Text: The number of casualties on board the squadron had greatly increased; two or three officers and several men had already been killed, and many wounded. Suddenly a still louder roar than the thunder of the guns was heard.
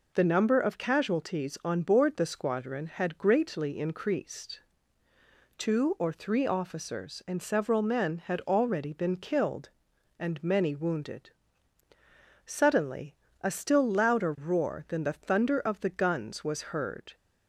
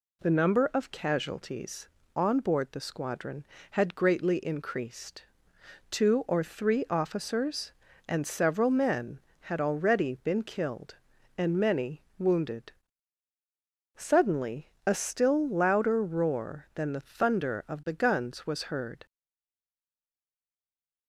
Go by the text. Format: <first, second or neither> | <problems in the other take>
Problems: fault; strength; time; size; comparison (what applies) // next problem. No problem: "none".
first | pauses between "many" and "wounded"; slight; at 12.0 s; 0.16 s long // pauses between "Suddenly" and "a"; slight; at 14.6 s; 0.18 s long; slight in the first // stays silent after the last word; noticeable; from 19.0 s on; 2.0 s long